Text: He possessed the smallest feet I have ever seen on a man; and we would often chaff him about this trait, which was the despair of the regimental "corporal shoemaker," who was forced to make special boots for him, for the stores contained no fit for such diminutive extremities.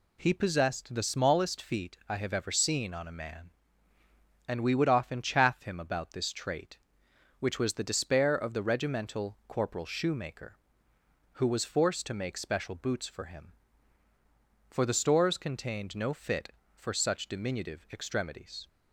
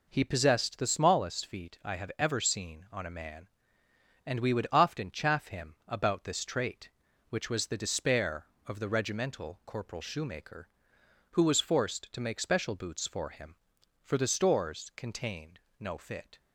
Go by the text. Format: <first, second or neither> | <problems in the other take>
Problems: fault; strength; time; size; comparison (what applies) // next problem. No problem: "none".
first | pauses between "contained" and "no"; slight; at 15.5 s; 0.18 s long // stops before "for such diminutive extremities"; at 16.3 s